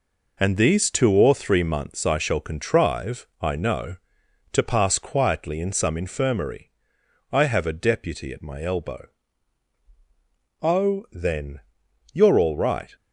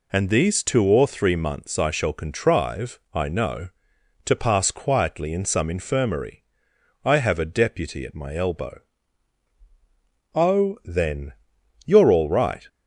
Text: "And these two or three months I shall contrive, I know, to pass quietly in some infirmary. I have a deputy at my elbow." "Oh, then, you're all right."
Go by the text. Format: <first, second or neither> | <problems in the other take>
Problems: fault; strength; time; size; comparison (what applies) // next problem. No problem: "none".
second | gets quieter; noticeable; throughout; 6 dB